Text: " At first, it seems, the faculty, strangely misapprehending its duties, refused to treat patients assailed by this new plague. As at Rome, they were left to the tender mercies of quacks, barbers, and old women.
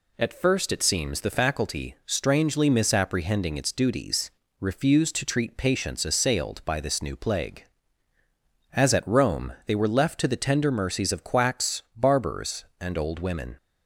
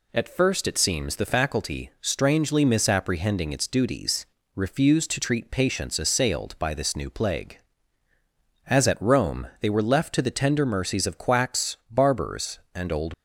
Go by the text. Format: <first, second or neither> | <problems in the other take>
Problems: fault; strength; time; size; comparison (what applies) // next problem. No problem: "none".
first | stops before "women"; at 13.1 s